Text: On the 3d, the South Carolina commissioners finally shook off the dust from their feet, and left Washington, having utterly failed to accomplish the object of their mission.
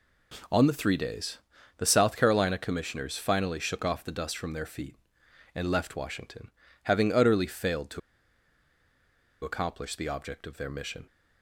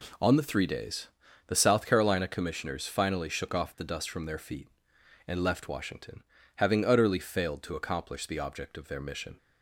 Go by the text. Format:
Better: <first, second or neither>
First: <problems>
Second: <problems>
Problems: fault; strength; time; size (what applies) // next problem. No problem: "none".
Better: second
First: pauses between "to" and "accomplish"; strong; at 7.9 s; 1.4 s long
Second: none